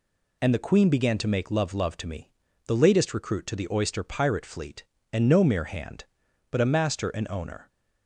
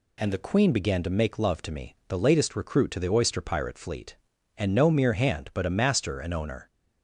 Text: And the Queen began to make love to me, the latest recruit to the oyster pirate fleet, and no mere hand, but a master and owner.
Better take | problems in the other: second | says "love" twice; at 1.7 s

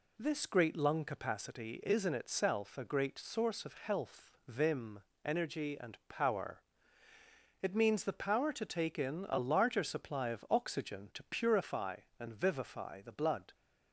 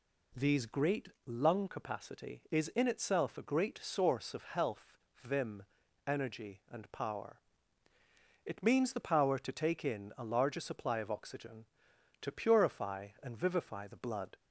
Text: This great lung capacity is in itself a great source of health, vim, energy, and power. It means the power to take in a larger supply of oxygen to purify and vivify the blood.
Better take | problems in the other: first | says "These" for "This"; at 0.3 s // pauses between "great" and "lung"; slight; at 1.0 s; 0.18 s long

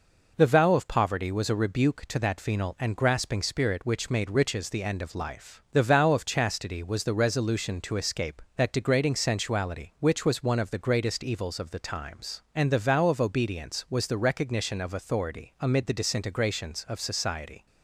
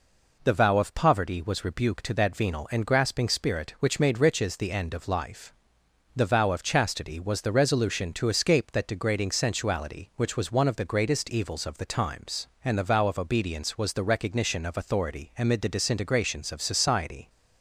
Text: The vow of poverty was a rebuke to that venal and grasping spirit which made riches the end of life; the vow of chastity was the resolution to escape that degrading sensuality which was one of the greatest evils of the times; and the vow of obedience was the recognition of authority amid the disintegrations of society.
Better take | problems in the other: first | skips "a"; at 1.6 s

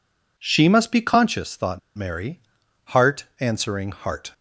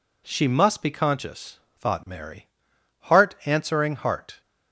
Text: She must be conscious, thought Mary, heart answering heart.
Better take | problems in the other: second | pauses between "thought" and "Mary"; slight; at 1.7 s; 0.17 s long

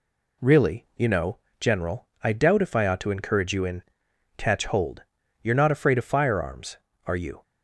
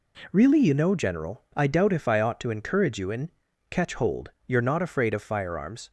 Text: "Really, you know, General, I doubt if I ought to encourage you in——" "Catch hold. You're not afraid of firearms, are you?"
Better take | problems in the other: first | stops before "are you"; at 5.8 s

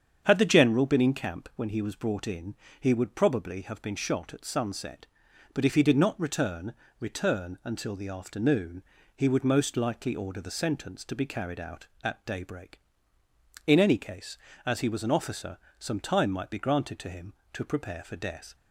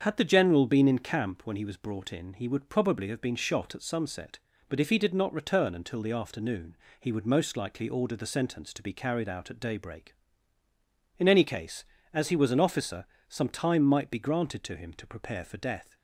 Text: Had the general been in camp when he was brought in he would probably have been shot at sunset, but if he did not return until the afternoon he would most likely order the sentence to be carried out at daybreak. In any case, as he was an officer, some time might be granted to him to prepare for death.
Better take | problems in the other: second | starts louder than the rest; strong; until 1.2 s; 7.5 dB; also in the second // pauses between "in" and "he"; slight; at 2.5 s; 0.24 s long // says "return" twice; at 7.0 s // pauses between "afternoon" and "he"; slight; at 8.8 s; 0.30 s long; slight in the second

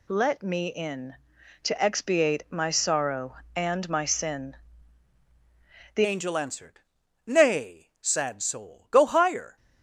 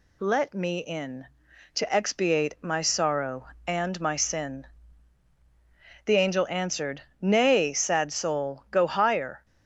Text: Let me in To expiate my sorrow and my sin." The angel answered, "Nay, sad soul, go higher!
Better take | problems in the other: second | changes voice at "angel"; from 6.0 s on; 3.5 s long

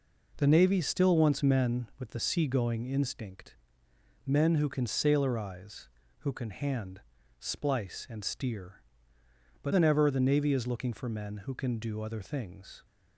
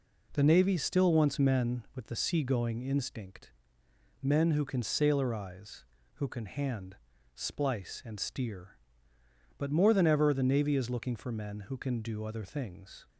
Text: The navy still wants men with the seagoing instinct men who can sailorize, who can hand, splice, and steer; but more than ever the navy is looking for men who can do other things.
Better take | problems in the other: second | pauses between "instinct" and "men"; noticeable; at 3.5 s; 0.72 s long; noticeable in the second // skips "more"; at 9.7 s

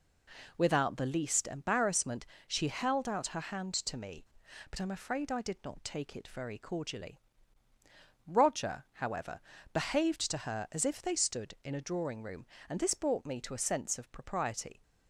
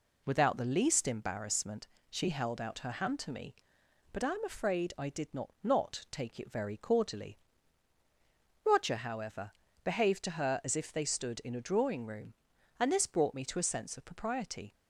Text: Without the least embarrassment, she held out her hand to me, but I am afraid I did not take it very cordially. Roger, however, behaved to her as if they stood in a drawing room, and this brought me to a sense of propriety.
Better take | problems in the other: first | says "not" twice; at 5.6 s

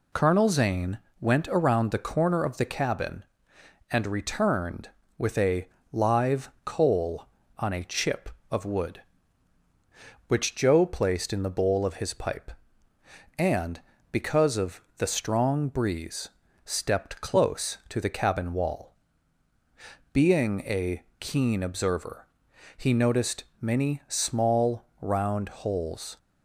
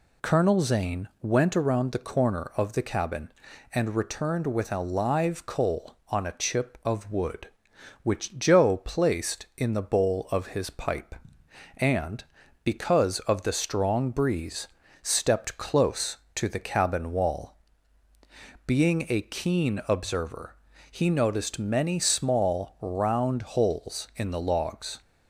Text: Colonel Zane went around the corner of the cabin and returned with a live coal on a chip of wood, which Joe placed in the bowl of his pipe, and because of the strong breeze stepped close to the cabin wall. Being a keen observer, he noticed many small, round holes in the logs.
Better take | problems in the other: second | pauses between "Zane" and "went"; slight; at 0.9 s; 0.20 s long // pauses between "a" and "live"; slight; at 5.6 s; 0.24 s long // pauses between "of" and "the"; slight; at 14.8 s; 0.16 s long // pauses between "breeze" and "stepped"; slight; at 16.2 s; 0.34 s long; slight in the second // pauses between "a" and "keen"; slight; at 21.0 s; 0.18 s long // stops before "in the logs"; at 26.1 s

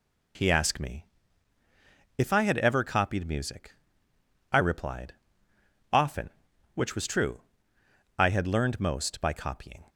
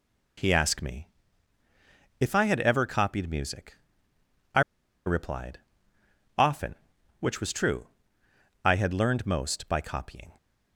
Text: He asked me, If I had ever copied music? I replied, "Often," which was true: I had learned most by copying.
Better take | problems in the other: first | pauses between "I" and "replied"; at 4.6 s; 0.45 s long

